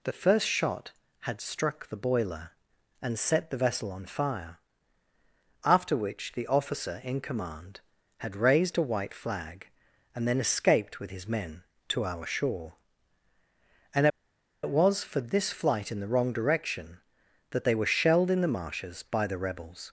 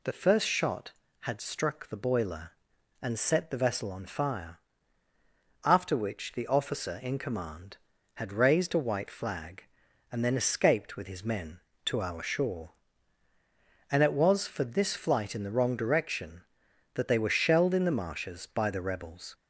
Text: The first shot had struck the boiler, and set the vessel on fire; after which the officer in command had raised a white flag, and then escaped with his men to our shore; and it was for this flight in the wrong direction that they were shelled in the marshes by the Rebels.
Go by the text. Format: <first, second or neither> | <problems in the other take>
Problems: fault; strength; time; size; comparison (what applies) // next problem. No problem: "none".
second | pauses between "and" and "it"; noticeable; at 14.0 s; 0.56 s long